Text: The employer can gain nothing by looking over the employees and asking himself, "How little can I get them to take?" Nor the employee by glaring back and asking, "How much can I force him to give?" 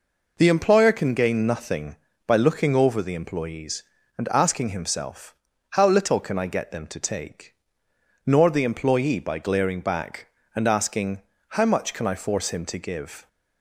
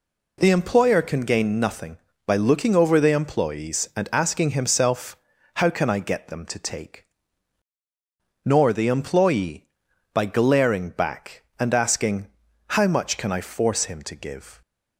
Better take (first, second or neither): first